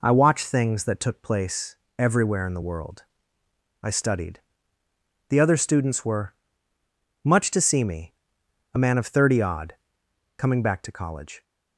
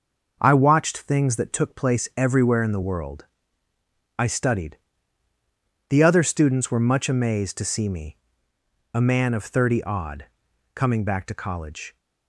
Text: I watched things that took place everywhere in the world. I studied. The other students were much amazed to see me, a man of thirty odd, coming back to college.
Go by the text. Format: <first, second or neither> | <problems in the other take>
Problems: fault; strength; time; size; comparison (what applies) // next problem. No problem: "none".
second | pauses between "place" and "everywhere"; slight; at 1.7 s; 0.22 s long // pauses between "were" and "much"; noticeable; at 6.3 s; 0.90 s long // skips "amazed"; at 7.4 s